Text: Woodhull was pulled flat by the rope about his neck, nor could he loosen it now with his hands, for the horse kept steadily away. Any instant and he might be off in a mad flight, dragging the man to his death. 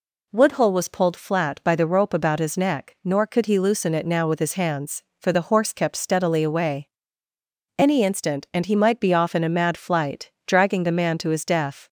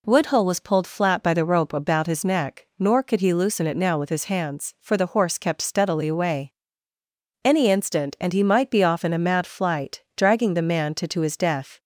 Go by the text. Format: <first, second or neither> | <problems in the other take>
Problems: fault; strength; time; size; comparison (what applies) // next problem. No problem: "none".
first | says "to" twice; at 11.0 s